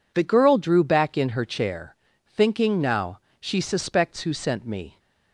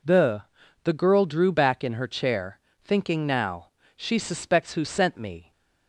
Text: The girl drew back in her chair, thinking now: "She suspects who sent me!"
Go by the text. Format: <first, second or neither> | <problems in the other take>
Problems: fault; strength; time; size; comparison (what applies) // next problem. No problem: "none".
first | says "The" twice; at 0.8 s